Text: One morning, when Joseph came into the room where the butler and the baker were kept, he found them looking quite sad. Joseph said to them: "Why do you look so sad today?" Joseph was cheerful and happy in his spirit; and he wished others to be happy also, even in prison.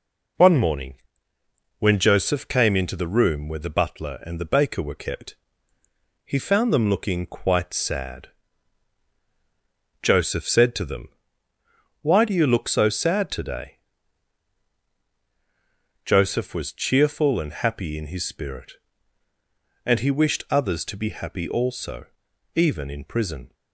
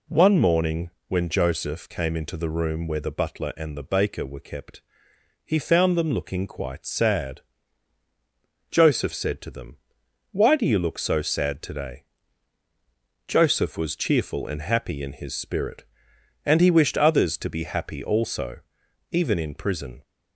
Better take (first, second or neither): neither